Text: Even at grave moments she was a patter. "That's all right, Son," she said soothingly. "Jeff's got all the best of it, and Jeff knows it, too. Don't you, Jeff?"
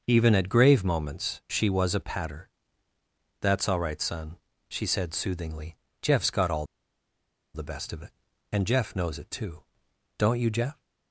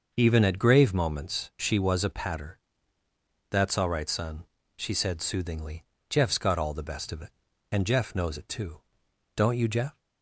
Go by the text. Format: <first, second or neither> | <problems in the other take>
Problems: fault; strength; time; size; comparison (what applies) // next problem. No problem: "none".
second | starts louder than the rest; noticeable; until 1.0 s; 6 dB; noticeable in the second // pauses between "all" and "the"; noticeable; at 6.6 s; 0.89 s long